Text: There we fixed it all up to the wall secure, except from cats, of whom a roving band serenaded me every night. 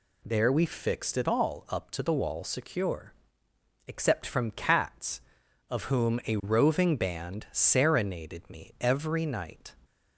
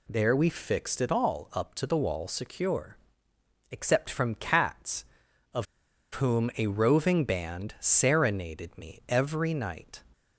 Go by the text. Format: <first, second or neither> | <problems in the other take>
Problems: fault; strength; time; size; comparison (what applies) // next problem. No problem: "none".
first | pauses between "of" and "whom"; noticeable; at 5.6 s; 0.48 s long